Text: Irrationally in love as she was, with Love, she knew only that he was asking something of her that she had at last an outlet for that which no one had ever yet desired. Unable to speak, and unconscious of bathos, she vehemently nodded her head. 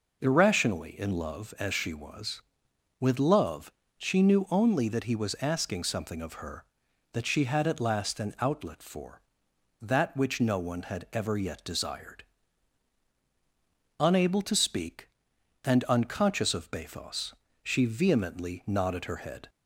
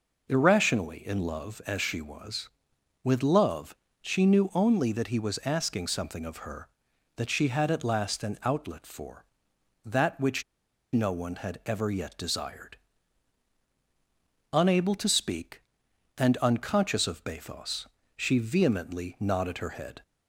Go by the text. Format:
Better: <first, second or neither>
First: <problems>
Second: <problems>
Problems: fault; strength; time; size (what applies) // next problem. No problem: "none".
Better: first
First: none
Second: pauses between "which" and "no"; noticeable; at 10.4 s; 0.50 s long